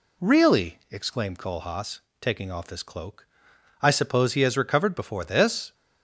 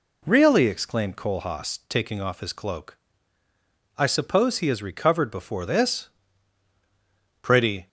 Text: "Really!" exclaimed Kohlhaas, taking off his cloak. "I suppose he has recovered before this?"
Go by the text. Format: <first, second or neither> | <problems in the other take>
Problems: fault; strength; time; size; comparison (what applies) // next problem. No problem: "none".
first | goes on to say "Pretty"; slight; from 7.4 s on; 0.46 s long